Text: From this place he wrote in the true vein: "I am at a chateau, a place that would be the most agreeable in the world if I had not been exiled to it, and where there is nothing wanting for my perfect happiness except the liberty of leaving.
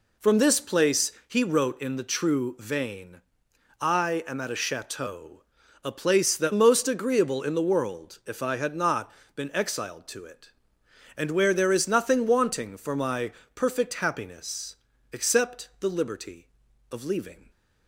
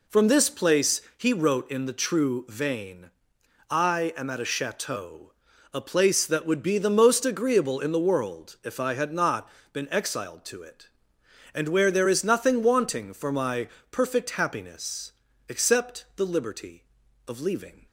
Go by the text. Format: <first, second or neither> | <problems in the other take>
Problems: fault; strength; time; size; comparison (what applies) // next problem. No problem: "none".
second | pauses between "place" and "he"; slight; at 1.1 s; 0.16 s long; slight in the second // skips "would be the"; at 6.5 s // pauses between "not" and "been"; slight; at 9.1 s; 0.24 s long; slight in the second // pauses between "my" and "perfect"; slight; at 13.3 s; 0.22 s long; slight in the second // pauses between "happiness" and "except"; at 14.7 s; 0.38 s long; also in the second